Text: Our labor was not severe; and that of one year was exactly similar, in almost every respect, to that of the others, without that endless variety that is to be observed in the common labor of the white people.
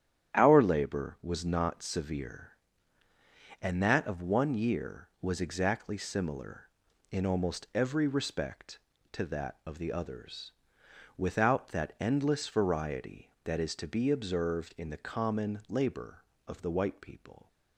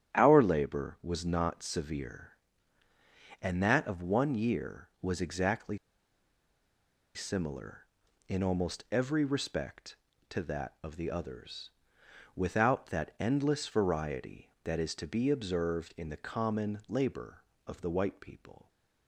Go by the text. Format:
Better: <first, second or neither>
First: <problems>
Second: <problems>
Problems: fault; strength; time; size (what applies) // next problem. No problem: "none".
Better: first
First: starts louder than the rest; strong; until 1.3 s; 10.5 dB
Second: starts louder than the rest; strong; until 1.1 s; 10.5 dB // pauses between "exactly" and "similar"; strong; at 5.7 s; 1.3 s long